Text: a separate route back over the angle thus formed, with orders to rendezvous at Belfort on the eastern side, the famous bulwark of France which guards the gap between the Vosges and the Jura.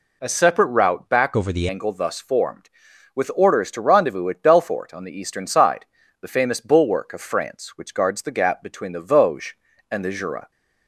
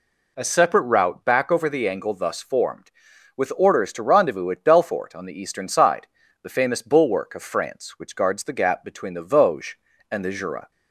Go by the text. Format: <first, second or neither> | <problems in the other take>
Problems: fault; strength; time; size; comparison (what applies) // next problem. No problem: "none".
second | changes voice from "over" to "the"; from 1.3 to 1.6 s; 0.3 s long